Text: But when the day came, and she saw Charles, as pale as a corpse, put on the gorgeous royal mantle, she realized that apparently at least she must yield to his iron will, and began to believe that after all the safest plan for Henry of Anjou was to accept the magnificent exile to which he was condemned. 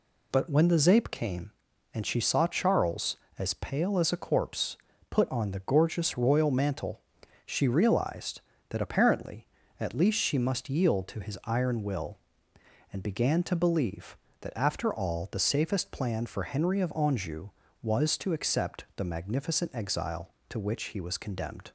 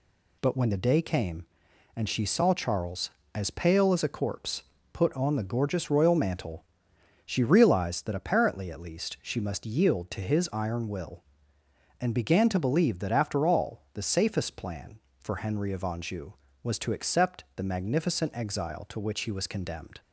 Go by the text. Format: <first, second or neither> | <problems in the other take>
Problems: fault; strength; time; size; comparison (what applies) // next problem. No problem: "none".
second | says "zape" for "day"; at 0.7 s